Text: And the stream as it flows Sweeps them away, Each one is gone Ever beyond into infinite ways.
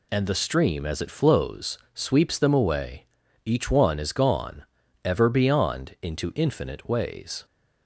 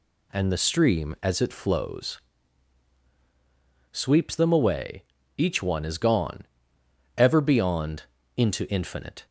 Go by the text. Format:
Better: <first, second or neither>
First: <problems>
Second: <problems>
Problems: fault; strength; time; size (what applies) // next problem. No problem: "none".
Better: first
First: pauses between "flows" and "Sweeps"; slight; at 1.7 s; 0.18 s long // pauses between "gone" and "Ever"; at 4.6 s; 0.42 s long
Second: pauses between "flows" and "Sweeps"; strong; at 2.1 s; 1.7 s long // pauses between "gone" and "Ever"; noticeable; at 6.4 s; 0.72 s long // pauses between "beyond" and "into"; slight; at 8.0 s; 0.34 s long // stops before "ways"; at 9.2 s